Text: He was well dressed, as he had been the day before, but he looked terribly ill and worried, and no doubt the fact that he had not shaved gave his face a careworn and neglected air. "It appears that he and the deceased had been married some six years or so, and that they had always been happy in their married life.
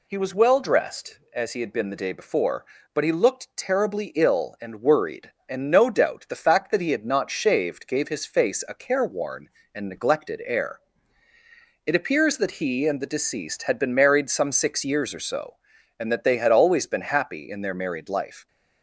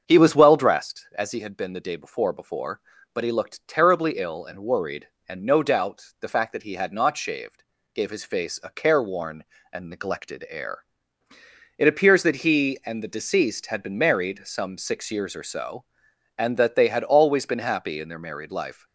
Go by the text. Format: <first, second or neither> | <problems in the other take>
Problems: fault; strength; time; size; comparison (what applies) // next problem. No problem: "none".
first | starts louder than the rest; until 1.0 s; 7 dB // says "before" twice; at 2.3 s // pauses between "shaved" and "gave"; slight; at 7.6 s; 0.32 s long